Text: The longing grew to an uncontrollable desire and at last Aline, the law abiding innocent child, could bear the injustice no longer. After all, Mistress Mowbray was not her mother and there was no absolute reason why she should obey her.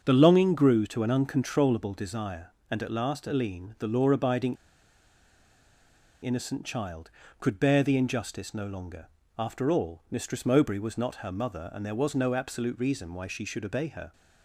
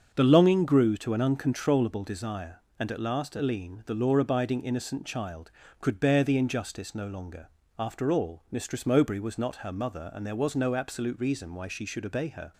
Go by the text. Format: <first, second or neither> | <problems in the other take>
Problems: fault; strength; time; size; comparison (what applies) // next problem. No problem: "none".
second | starts louder than the rest; until 1.0 s; 6.5 dB; also in the second // pauses between "abiding" and "innocent"; strong; at 4.5 s; 1.6 s long